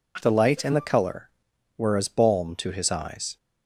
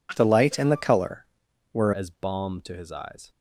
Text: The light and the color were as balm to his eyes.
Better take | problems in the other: first | changes voice at "as"; from 1.9 s on; 1.3 s long

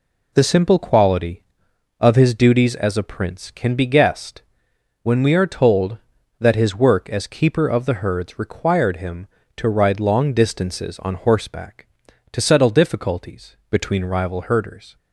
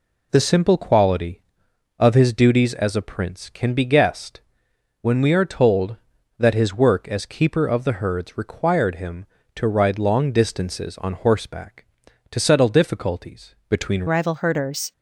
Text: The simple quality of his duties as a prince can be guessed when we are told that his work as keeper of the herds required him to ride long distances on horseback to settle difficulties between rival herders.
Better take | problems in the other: first | pauses between "guessed" and "when"; noticeable; at 4.3 s; 0.62 s long; noticeable in the first // changes voice at "rival"; from 14.0 s on; 0.9 s long

